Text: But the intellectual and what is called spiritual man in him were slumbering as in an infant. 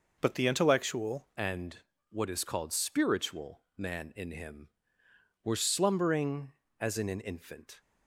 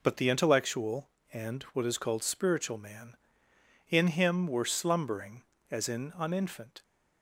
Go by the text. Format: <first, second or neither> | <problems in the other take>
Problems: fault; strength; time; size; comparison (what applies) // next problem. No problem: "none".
second | changes voice at "and"; from 1.3 s on; 6.4 s long // pauses between "and" and "what"; slight; at 1.7 s; 0.32 s long